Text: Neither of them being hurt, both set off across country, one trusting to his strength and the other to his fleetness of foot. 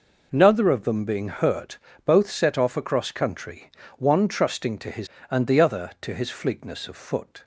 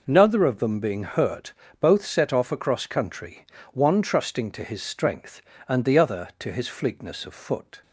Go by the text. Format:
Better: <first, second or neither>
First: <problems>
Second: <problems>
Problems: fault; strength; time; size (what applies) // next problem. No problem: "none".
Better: second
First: skips "strength"; at 5.1 s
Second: none